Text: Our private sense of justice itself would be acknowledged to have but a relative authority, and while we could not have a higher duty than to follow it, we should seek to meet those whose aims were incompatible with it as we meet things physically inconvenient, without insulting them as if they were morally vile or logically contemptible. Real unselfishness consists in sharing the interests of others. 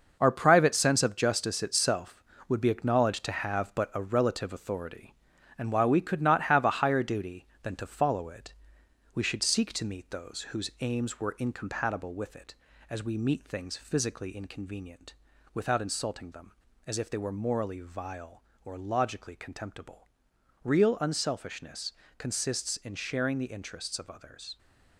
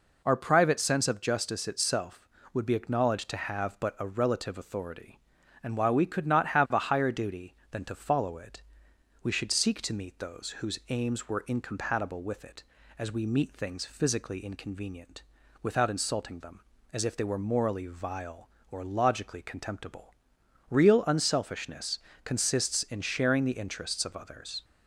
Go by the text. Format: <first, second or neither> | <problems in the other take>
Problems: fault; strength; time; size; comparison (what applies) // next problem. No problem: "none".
second | gets quieter; strong; throughout; 8.5 dB // pauses between "unselfishness" and "consists"; slight; at 21.9 s; 0.26 s long; slight in the second